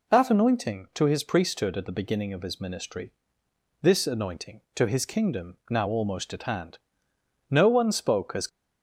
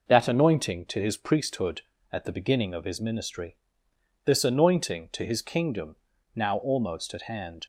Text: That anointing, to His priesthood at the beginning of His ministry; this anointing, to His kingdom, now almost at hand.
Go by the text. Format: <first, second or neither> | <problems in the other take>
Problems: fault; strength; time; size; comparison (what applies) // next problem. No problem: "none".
second | goes on to say "No one spoke as"; noticeable; from 7.4 s on; 0.98 s long